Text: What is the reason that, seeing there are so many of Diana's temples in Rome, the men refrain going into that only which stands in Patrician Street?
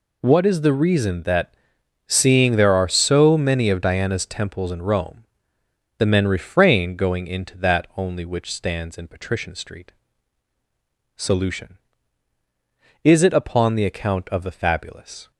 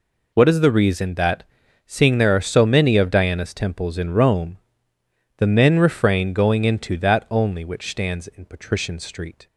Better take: second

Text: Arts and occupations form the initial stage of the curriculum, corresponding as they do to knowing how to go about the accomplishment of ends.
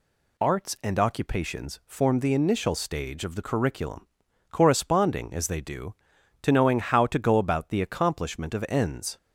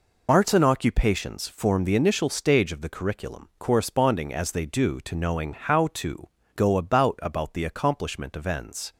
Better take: first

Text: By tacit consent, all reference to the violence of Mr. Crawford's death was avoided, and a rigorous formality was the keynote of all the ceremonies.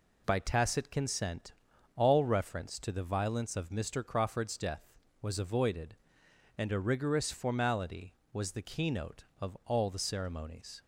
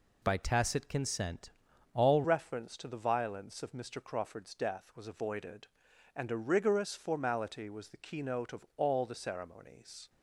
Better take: first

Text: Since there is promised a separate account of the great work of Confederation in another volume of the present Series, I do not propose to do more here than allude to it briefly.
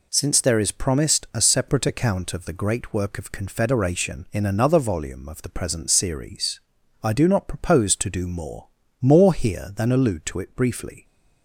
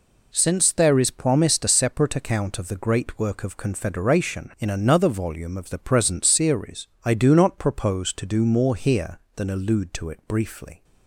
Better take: second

